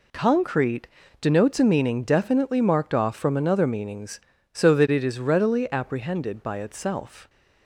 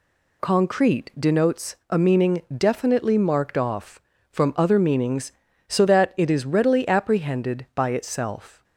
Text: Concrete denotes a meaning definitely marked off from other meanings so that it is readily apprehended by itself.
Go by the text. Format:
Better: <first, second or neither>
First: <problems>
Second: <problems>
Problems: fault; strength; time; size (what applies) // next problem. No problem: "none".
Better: second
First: pauses between "Concrete" and "denotes"; slight; at 0.8 s; 0.32 s long // says "another" for "other"; at 3.3 s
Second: none